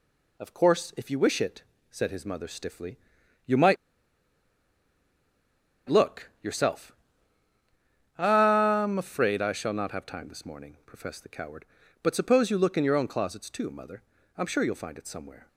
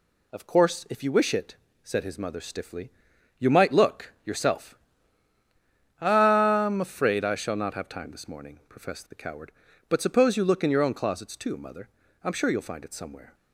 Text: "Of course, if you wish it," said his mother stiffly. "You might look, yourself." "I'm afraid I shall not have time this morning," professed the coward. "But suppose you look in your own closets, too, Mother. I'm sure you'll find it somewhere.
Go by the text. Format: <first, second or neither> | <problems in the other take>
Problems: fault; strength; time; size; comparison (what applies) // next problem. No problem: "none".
second | pauses between "might" and "look"; strong; at 3.7 s; 2.1 s long